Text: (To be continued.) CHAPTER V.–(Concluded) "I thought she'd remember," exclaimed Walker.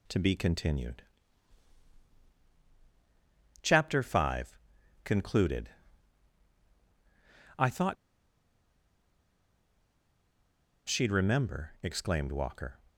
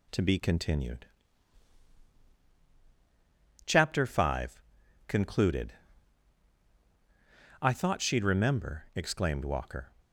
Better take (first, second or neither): second